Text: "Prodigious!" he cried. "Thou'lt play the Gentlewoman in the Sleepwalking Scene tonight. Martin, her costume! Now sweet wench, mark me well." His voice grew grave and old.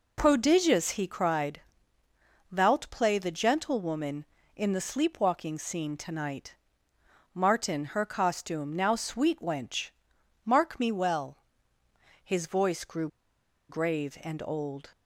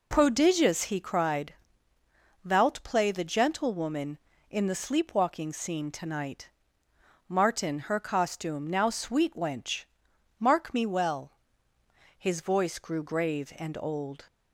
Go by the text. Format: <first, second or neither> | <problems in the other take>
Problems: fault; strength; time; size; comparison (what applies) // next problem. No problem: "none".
second | pauses between "grew" and "grave"; noticeable; at 13.0 s; 0.62 s long